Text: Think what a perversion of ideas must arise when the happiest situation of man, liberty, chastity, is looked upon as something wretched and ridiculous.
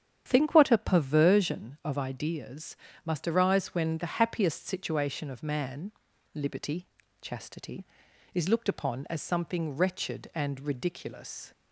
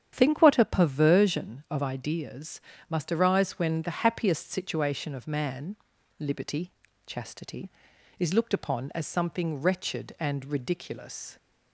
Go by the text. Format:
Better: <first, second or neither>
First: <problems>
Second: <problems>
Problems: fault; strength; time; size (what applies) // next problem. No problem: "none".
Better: neither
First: starts louder than the rest; strong; until 1.2 s; 8.5 dB // pauses between "ideas" and "must"; slight; at 2.7 s; 0.30 s long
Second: starts louder than the rest; strong; until 1.1 s; 9 dB // pauses between "ideas" and "must"; slight; at 2.5 s; 0.30 s long